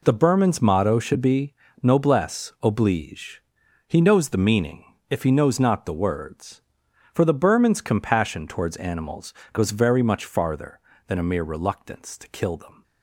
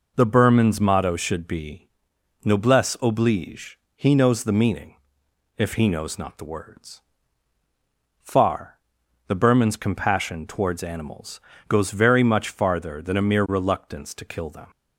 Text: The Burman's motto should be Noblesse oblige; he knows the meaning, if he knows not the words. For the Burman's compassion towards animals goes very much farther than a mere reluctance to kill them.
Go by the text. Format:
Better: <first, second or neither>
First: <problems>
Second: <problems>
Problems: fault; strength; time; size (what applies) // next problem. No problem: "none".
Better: first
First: pauses between "be" and "Noblesse"; slight; at 1.5 s; 0.28 s long // pauses between "animals" and "goes"; slight; at 9.3 s; 0.20 s long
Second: pauses between "be" and "Noblesse"; noticeable; at 1.8 s; 0.56 s long // says "Far" for "For"; at 8.2 s // pauses between "animals" and "goes"; slight; at 11.4 s; 0.28 s long